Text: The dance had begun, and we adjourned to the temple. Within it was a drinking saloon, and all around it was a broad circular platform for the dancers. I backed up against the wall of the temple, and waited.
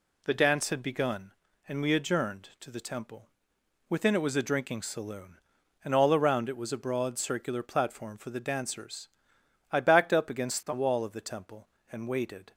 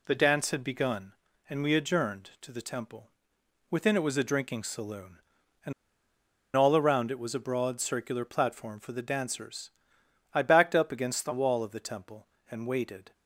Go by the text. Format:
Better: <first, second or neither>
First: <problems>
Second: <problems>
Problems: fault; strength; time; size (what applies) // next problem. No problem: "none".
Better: first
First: none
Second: pauses between "and" and "all"; noticeable; at 5.7 s; 0.83 s long